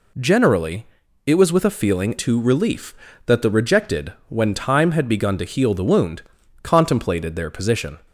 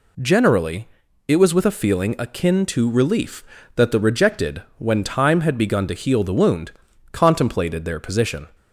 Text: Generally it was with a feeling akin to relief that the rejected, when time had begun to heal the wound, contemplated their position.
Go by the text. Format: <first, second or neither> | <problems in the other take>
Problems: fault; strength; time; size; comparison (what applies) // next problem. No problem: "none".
second | pauses between "Generally" and "it"; at 0.8 s; 0.38 s long; also in the second // skips "akin"; at 2.1 s